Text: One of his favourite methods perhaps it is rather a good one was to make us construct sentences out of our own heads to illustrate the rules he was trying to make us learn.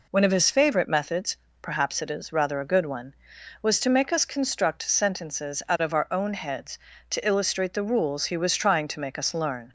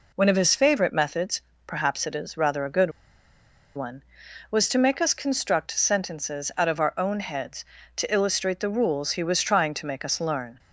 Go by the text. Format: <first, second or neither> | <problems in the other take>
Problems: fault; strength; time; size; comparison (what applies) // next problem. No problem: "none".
first | pauses between "methods" and "perhaps"; slight; at 1.4 s; 0.24 s long; slight in the first // pauses between "good" and "one"; noticeable; at 2.9 s; 0.85 s long